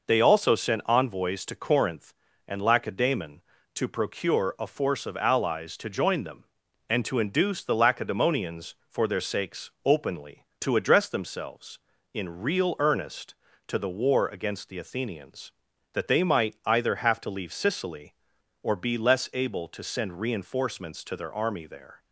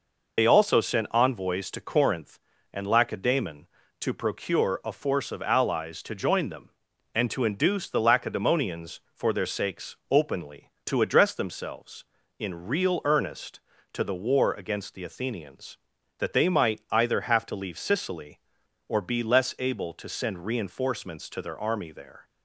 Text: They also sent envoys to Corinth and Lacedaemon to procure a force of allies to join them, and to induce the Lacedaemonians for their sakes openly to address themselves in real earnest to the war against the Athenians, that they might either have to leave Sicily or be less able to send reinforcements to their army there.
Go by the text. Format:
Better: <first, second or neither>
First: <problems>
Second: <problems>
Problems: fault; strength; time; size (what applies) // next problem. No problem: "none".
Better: first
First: none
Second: loses the start of "They"; at 0.3 s; 55 ms